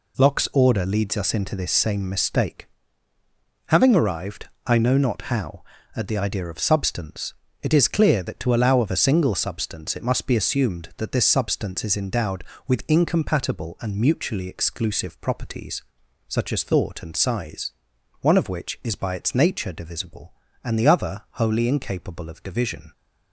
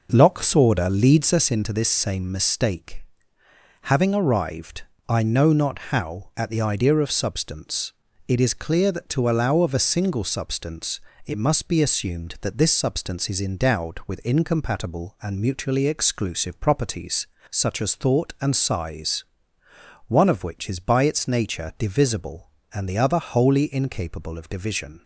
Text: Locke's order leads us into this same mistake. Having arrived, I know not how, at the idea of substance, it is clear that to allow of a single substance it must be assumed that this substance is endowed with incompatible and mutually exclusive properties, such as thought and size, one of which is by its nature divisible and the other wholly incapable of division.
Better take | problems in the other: first | starts louder than the rest; noticeable; until 1.5 s; 5.5 dB // pauses between "substance" and "it"; slight; at 10.9 s; 0.28 s long

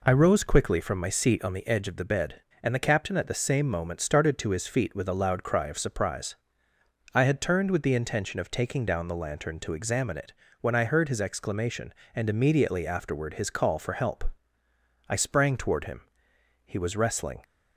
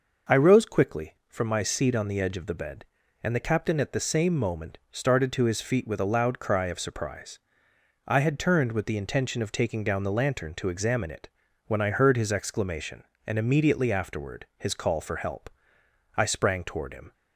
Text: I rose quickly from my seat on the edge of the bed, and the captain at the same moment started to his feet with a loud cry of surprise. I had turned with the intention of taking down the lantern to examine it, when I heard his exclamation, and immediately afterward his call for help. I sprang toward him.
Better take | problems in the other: second | goes on to say "He was wrestling"; noticeable; from 16.6 s on; 0.78 s long

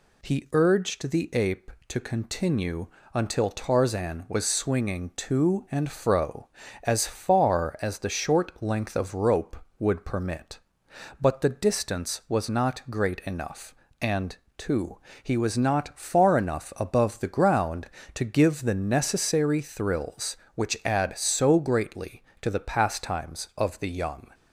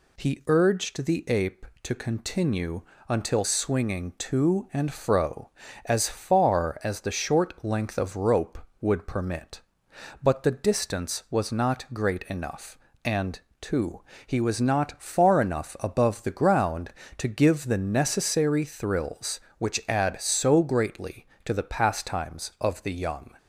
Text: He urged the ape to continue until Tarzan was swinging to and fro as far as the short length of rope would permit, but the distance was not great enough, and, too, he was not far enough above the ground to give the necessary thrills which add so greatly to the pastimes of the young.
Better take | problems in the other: first | pauses between "continue" and "until"; slight; at 2.8 s; 0.26 s long; slight in the first // skips "Tarzan was"; at 3.4 s

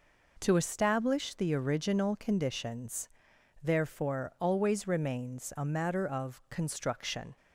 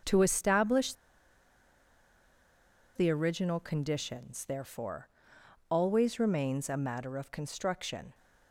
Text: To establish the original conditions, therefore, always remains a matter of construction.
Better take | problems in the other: first | pauses between "establish" and "the"; strong; at 0.9 s; 2.0 s long

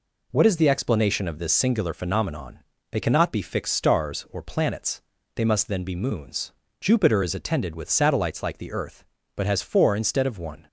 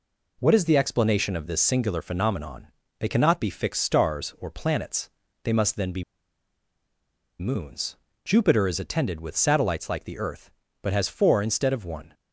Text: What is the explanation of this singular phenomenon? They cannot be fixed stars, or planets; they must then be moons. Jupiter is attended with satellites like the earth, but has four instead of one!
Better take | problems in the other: first | pauses between "be" and "moons"; strong; at 6.0 s; 1.3 s long

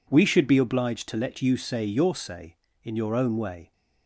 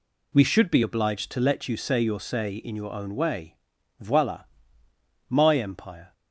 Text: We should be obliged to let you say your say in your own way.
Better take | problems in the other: first | goes on to say "Voila my empire"; strong; from 4.0 s on; 2.1 s long

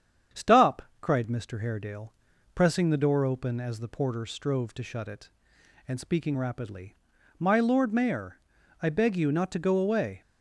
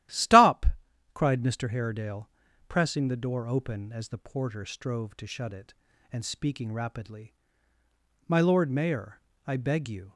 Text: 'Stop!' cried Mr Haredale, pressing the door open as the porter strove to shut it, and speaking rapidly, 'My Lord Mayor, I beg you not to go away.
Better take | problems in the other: first | starts louder than the rest; strong; until 1.6 s; 13.5 dB; strong in the first // stops before "not to go away"; at 10.1 s

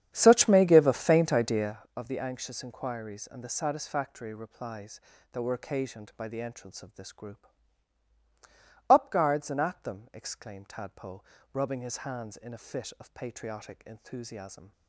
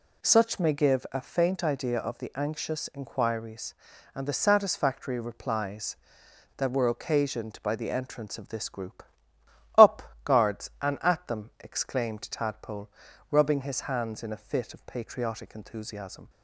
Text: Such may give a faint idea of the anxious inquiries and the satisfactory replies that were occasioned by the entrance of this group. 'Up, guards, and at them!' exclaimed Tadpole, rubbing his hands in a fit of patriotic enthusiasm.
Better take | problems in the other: second | starts louder than the rest; strong; until 1.9 s; 9 dB

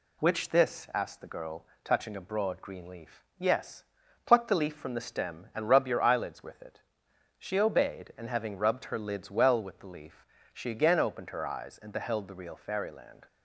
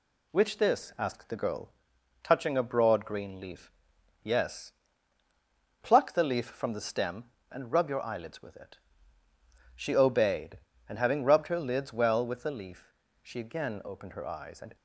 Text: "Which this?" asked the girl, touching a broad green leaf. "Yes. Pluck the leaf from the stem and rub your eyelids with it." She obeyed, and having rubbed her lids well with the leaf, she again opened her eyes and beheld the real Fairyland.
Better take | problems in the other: first | stops before "beheld the real Fairyland"; at 14.7 s

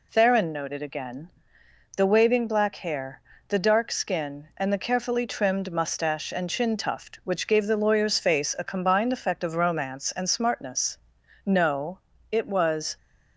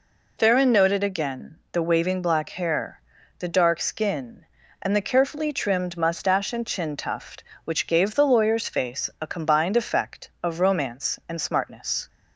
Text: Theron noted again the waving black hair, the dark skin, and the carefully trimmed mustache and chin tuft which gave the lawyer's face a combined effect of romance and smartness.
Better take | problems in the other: second | pauses between "again" and "the"; noticeable; at 1.2 s; 0.66 s long // goes on to say "No it was"; from 11.4 s on; 1.5 s long

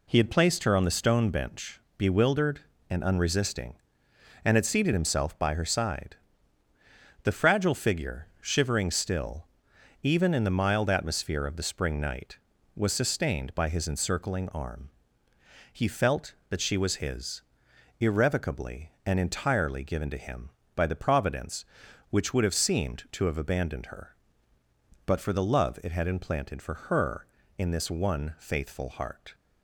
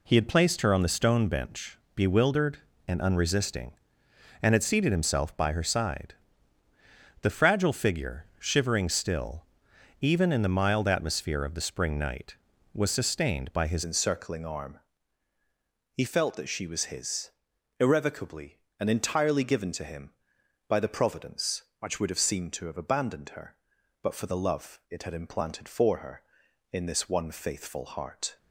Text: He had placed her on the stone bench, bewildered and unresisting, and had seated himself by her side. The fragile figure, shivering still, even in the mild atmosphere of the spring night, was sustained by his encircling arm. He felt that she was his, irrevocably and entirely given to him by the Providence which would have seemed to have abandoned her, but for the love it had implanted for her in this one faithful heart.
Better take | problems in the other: first | changes voice at "encircling"; from 13.8 s on; 14.5 s long

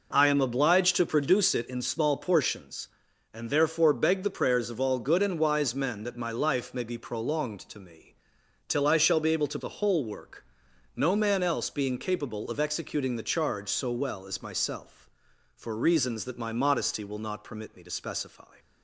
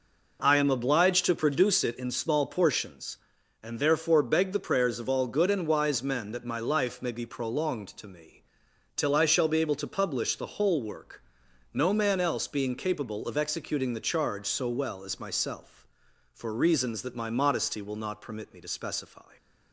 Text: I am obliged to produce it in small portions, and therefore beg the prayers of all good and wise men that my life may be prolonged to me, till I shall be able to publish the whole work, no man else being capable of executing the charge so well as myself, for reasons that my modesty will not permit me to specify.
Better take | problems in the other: second | skips "publish"; at 9.5 s

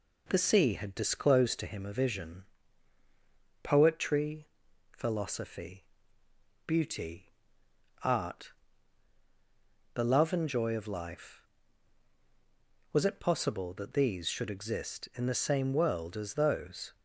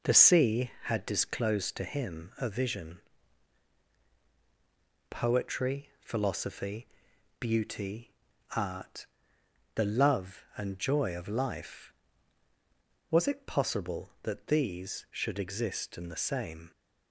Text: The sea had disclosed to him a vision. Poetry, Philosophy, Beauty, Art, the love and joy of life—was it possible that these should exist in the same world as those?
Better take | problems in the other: first | stops before "world as those"; at 16.7 s

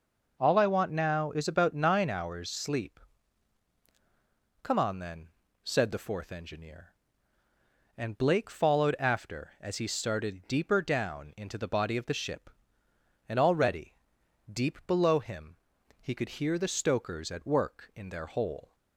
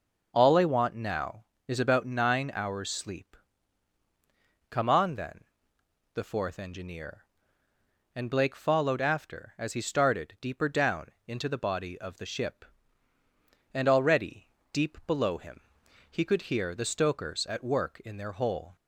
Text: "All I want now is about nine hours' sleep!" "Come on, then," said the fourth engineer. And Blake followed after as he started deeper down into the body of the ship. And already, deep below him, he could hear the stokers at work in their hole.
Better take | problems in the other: first | skips "said"; at 5.8 s // pauses between "down" and "into"; slight; at 11.0 s; 0.20 s long

